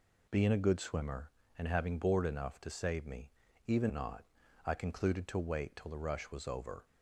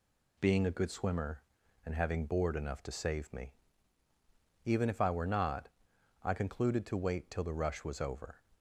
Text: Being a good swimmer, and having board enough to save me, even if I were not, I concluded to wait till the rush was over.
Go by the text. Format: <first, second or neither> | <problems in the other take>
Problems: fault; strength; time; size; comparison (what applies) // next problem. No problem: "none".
second | skips "if I were"; at 3.9 s